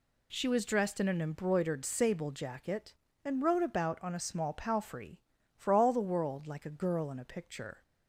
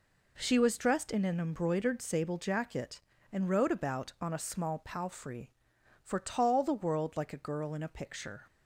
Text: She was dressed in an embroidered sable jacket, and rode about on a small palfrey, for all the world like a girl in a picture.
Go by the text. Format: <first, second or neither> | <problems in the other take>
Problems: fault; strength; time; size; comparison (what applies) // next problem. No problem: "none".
first | says "tall" for "all"; at 6.1 s